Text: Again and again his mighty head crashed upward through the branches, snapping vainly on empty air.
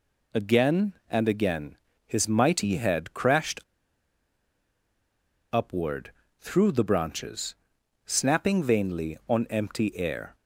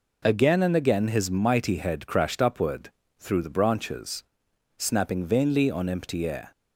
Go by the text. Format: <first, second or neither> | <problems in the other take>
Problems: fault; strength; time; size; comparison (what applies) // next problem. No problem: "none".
second | pauses between "again" and "his"; slight; at 1.7 s; 0.30 s long // pauses between "crashed" and "upward"; strong; at 3.5 s; 1.9 s long // pauses between "upward" and "through"; slight; at 6.1 s; 0.28 s long; slight in the second